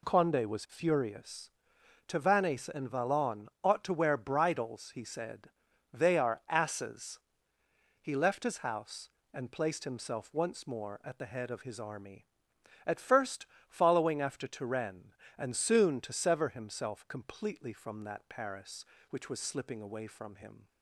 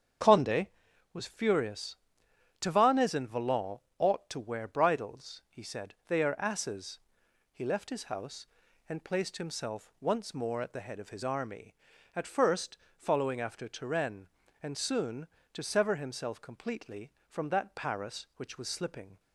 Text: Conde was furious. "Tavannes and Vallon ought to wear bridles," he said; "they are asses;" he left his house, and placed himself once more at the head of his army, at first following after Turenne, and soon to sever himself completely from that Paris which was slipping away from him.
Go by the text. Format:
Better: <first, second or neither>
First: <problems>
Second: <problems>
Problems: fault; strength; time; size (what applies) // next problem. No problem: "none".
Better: first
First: pauses between "first" and "following"; slight; at 13.4 s; 0.22 s long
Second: starts louder than the rest; strong; until 1.6 s; 7.5 dB // pauses between "Vallon" and "ought"; slight; at 3.7 s; 0.18 s long // pauses between "first" and "following"; slight; at 12.7 s; 0.22 s long // stops before "away from him"; at 19.1 s